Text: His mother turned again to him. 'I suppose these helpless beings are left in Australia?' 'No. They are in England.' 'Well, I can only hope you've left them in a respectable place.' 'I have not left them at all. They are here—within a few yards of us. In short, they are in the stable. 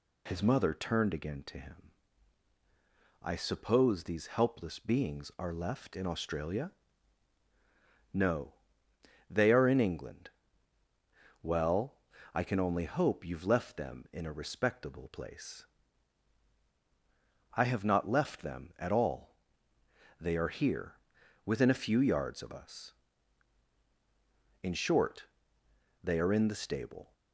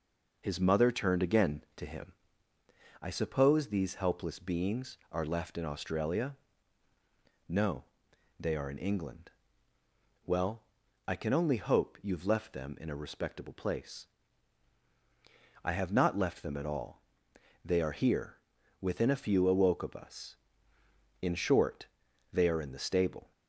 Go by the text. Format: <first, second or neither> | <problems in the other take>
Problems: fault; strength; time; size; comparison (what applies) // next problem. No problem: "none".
first | says "awoke" for "yards"; at 19.4 s